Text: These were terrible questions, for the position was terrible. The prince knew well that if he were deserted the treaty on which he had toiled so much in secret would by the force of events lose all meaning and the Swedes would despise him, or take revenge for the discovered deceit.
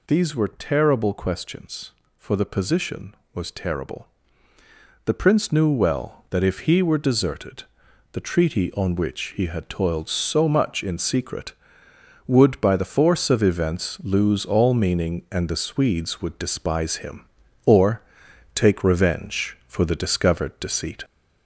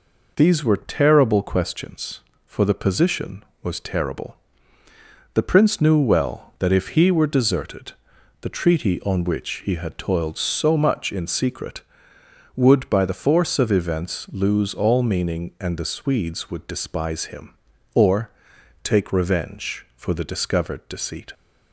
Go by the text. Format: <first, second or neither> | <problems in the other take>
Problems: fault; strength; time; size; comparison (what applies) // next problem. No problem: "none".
second | gets louder; throughout; 3.5 dB // pauses between "deserted" and "the"; noticeable; at 7.6 s; 0.46 s long; noticeable in the second // pauses between "or" and "take"; noticeable; at 18.0 s; 0.52 s long; noticeable in the second